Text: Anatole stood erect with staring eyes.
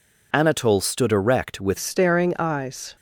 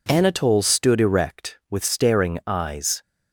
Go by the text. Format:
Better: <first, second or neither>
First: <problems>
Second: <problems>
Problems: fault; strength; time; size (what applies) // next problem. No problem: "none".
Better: second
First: changes voice at "staring"; from 1.7 s on; 1.2 s long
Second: none